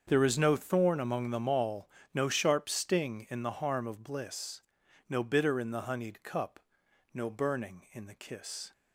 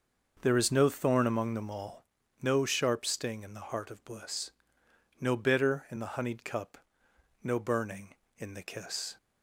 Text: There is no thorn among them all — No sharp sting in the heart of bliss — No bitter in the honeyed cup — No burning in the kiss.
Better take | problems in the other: second | starts louder than the rest; until 1.0 s; 7 dB; noticeable in the second // says "harm" for "heart"; at 3.5 s

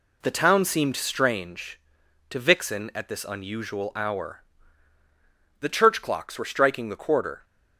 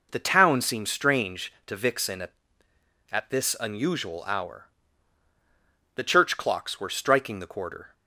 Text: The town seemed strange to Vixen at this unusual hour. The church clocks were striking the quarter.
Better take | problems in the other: first | says "at" twice; at 3.1 s

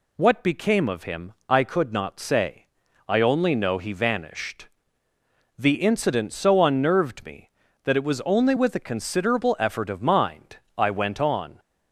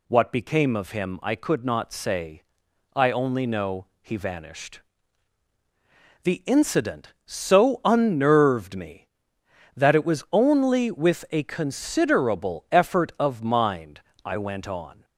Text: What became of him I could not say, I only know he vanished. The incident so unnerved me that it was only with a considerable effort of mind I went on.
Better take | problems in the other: neither | pauses between "mind" and "I"; slight; the same in both

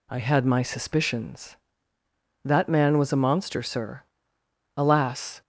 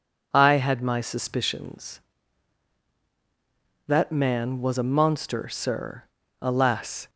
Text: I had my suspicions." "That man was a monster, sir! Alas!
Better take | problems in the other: neither | none

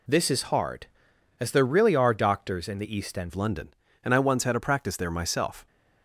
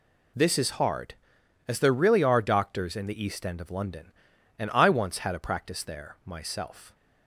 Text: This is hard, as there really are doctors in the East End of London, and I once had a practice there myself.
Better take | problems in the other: second | changes voice at "of"; from 3.2 s on; 2.4 s long

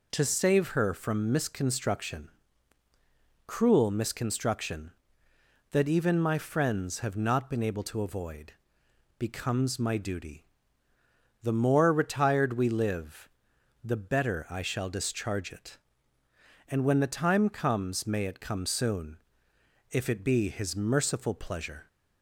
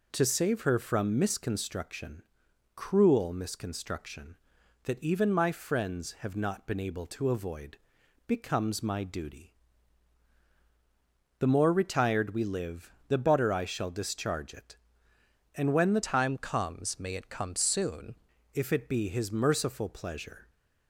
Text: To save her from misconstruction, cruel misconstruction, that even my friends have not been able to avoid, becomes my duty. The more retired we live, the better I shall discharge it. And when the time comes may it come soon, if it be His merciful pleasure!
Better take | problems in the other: first | changes voice from "time" to "soon"; from 16.0 to 18.1 s; 2.1 s long

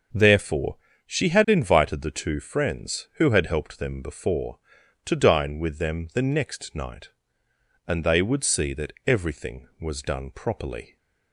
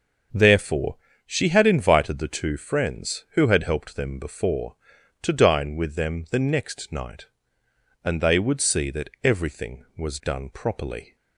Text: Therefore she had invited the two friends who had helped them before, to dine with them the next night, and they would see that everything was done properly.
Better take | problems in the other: neither | starts louder than the rest; the same in both // pauses between "Therefore" and "she"; slight; the same in both

